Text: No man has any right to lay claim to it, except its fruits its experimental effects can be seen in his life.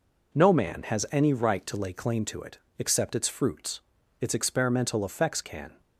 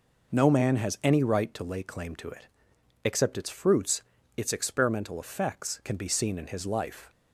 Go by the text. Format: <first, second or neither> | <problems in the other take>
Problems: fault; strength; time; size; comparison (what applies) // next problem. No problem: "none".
second | pauses between "fruits" and "its"; at 3.7 s; 0.40 s long; slight in the second // stops before "be seen in his life"; at 5.7 s